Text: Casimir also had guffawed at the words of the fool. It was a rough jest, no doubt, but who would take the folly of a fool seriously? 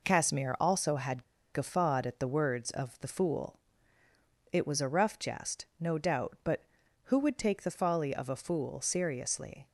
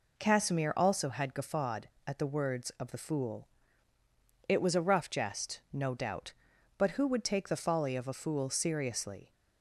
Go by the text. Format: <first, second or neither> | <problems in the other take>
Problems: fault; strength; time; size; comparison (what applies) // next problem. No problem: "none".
second | pauses between "had" and "guffawed"; slight; at 1.2 s; 0.30 s long